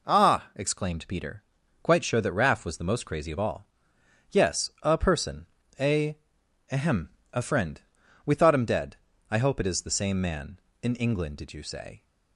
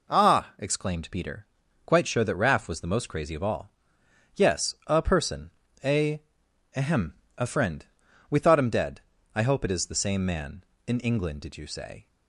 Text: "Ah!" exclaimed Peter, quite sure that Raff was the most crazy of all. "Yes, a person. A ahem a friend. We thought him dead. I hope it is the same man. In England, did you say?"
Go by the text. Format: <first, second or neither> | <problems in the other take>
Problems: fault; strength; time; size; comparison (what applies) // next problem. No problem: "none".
neither | pauses between "A" and "ahem"; noticeable; the same in both // pauses between "ahem" and "a"; slight; the same in both